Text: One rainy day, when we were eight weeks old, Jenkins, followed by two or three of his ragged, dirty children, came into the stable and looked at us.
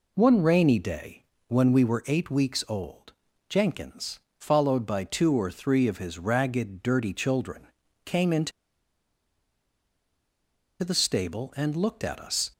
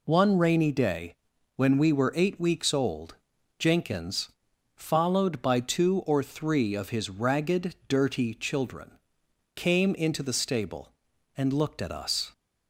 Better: second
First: pauses between "into" and "the"; strong; at 8.5 s; 2.3 s long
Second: none

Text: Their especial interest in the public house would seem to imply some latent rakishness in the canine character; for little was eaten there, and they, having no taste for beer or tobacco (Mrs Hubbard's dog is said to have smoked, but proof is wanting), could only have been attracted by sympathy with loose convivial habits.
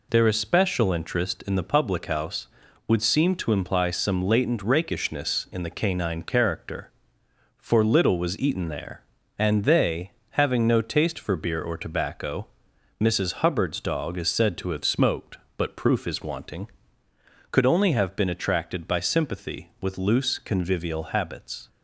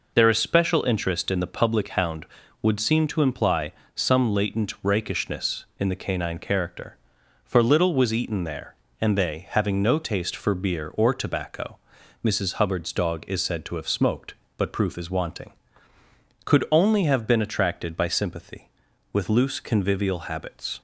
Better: first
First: none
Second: says "hound" for "house"; at 1.8 s // pauses between "imply" and "some"; slight; at 3.7 s; 0.22 s long

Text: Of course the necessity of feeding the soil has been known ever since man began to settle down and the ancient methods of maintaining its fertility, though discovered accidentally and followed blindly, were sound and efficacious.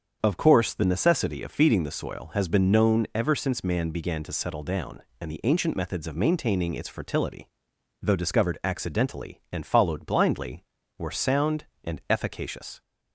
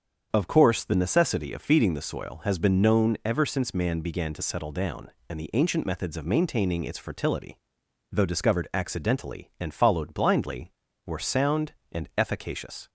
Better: neither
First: starts louder than the rest; strong; until 1.2 s; 7 dB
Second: starts louder than the rest; strong; until 1.3 s; 7 dB

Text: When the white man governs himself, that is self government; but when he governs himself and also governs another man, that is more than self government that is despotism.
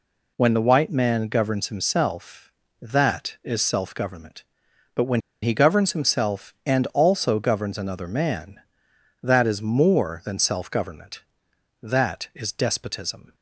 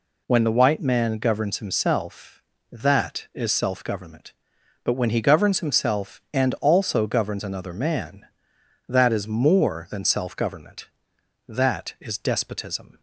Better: second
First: pauses between "when" and "he"; slight; at 5.2 s; 0.22 s long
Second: none

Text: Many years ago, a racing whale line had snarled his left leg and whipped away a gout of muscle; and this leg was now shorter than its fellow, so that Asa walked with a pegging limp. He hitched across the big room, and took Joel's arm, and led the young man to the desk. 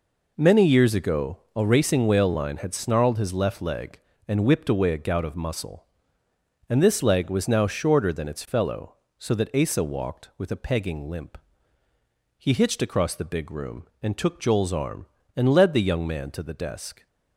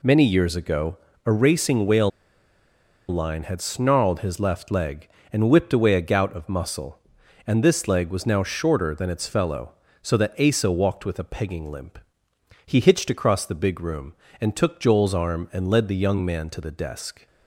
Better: first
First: none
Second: pauses between "whale" and "line"; at 2.1 s; 1.0 s long

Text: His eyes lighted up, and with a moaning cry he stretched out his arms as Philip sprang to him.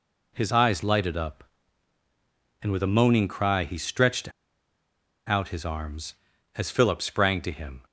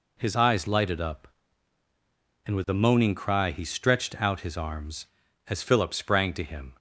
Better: second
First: pauses between "stretched" and "out"; noticeable; at 4.3 s; 0.97 s long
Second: none

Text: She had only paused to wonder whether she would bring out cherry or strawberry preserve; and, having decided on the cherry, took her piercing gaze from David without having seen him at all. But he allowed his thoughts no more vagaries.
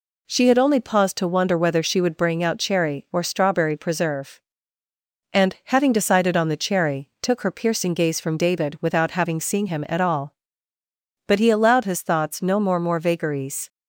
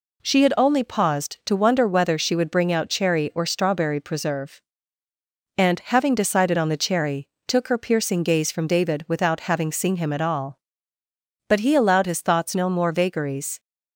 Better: second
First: says "more" twice; at 12.8 s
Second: none

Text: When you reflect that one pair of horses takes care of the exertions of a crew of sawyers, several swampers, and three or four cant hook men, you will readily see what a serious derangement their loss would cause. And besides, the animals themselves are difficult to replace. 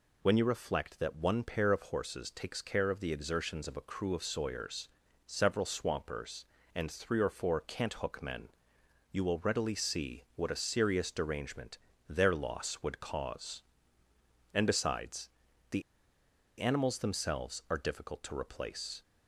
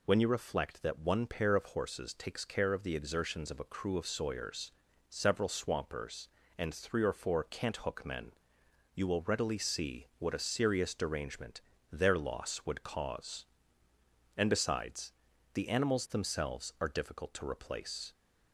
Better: second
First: pauses between "derangement" and "their"; slight; at 11.7 s; 0.28 s long // pauses between "the" and "animals"; noticeable; at 15.8 s; 0.78 s long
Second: pauses between "derangement" and "their"; slight; at 11.6 s; 0.28 s long

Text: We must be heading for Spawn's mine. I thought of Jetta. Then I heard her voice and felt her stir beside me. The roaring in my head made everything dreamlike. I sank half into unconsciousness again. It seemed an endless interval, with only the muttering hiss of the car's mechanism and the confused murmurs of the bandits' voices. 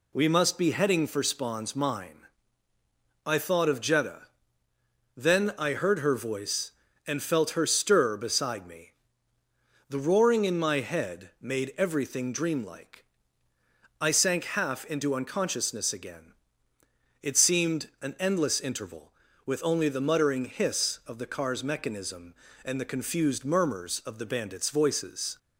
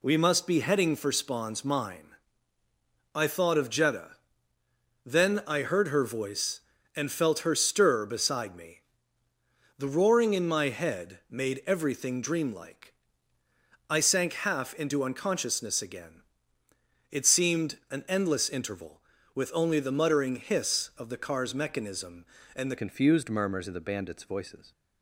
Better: first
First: none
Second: changes voice at "confused"; from 22.7 s on; 2.0 s long

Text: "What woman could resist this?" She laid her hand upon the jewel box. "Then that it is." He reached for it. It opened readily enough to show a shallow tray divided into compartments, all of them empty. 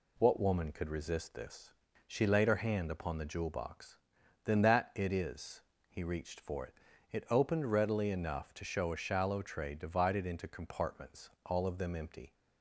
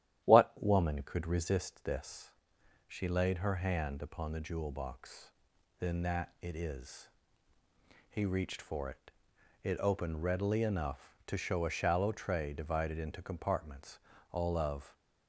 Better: first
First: none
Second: starts louder than the rest; strong; until 1.3 s; 12 dB // stops before "them empty"; at 14.9 s

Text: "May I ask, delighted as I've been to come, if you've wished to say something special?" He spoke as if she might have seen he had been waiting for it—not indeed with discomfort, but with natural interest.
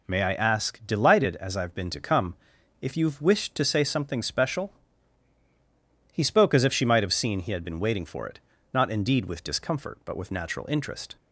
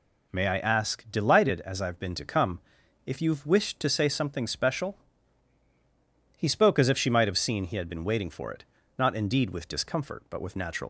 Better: first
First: none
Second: stops before "interest"; at 10.8 s

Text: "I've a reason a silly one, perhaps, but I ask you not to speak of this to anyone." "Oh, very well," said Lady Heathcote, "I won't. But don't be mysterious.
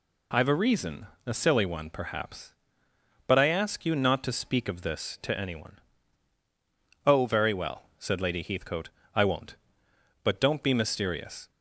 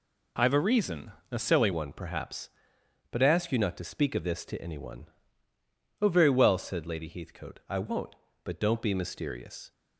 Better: first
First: pauses between "reason" and "a"; slight; at 1.0 s; 0.18 s long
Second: pauses between "reason" and "a"; slight; at 1.1 s; 0.18 s long // changes voice at "one"; from 1.7 s on; 8.0 s long

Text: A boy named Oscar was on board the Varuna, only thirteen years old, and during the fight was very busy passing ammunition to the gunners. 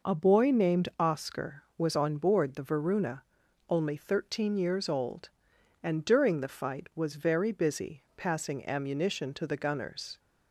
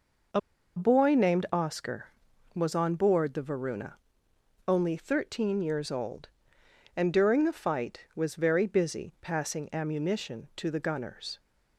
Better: first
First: none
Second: pauses between "A" and "boy"; at 0.3 s; 0.36 s long

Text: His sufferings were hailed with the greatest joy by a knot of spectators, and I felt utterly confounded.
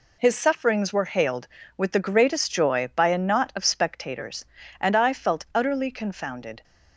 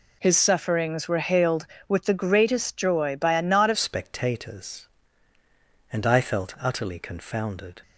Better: first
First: none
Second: changes voice at "spectators"; from 3.7 s on; 4.1 s long

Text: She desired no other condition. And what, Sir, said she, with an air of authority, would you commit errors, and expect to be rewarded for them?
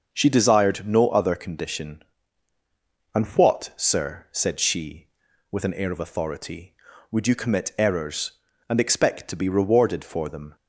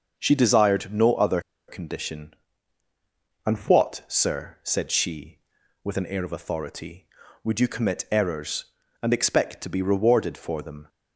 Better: first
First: none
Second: pauses between "other" and "condition"; slight; at 1.4 s; 0.27 s long

